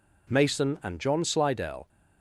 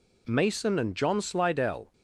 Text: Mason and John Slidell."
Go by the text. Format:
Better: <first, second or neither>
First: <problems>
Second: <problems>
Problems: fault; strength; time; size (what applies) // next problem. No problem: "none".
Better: neither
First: none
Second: none